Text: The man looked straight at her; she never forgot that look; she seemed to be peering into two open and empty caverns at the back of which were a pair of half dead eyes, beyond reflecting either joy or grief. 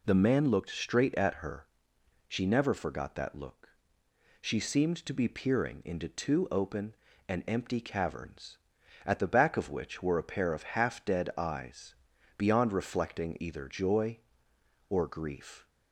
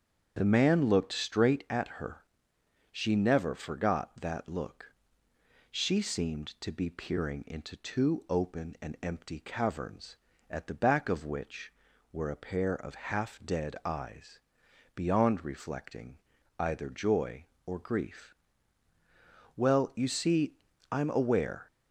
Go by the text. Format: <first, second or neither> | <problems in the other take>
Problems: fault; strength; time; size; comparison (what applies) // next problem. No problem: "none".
first | starts louder than the rest; strong; until 1.3 s; 7.5 dB // pauses between "reflecting" and "either"; at 16.1 s; 0.40 s long // goes on to say "Well you see I'm aware"; strong; from 19.5 s on; 2.1 s long